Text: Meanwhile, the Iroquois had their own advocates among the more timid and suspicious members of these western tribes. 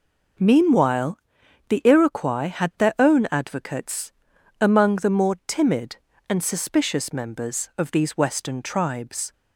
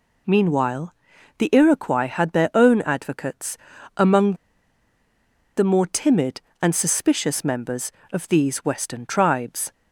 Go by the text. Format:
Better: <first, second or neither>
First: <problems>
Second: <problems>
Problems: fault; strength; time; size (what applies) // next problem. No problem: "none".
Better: first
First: pauses between "advocates" and "among"; noticeable; at 4.1 s; 0.48 s long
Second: pauses between "advocates" and "among"; at 3.5 s; 0.38 s long // pauses between "among" and "the"; at 4.3 s; 1.2 s long